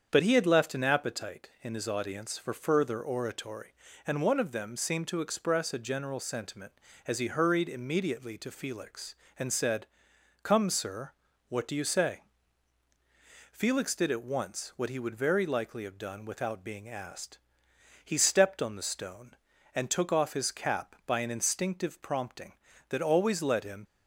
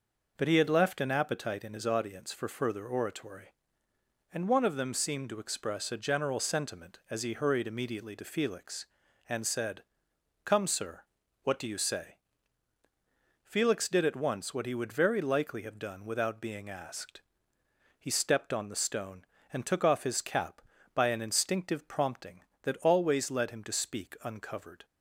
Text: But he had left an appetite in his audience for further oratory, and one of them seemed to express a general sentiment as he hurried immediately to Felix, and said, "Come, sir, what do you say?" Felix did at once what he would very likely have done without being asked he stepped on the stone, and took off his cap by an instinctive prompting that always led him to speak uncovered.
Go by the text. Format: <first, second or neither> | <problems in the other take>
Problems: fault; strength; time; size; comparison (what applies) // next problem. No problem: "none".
second | starts louder than the rest; strong; until 1.1 s; 7.5 dB // pauses between "asked" and "he"; noticeable; at 17.3 s; 0.68 s long; noticeable in the second // stops before "to speak uncovered"; at 23.8 s